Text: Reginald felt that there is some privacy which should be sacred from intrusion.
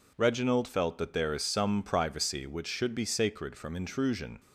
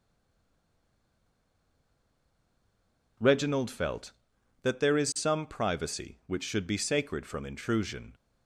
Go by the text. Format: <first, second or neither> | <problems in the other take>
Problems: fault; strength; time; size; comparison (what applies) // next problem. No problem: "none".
first | stays silent before the first word; strong; until 3.1 s; 3.1 s long